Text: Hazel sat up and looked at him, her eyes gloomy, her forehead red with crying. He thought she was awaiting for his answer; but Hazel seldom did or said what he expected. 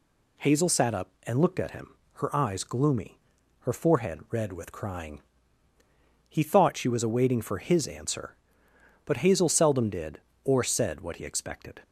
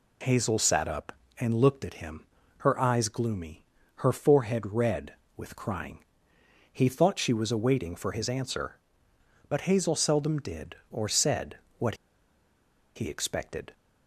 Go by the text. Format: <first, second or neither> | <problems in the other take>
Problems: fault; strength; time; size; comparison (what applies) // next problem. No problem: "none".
first | pauses between "said" and "what"; slight; at 11.5 s; 0.22 s long // pauses between "what" and "he"; at 11.9 s; 0.99 s long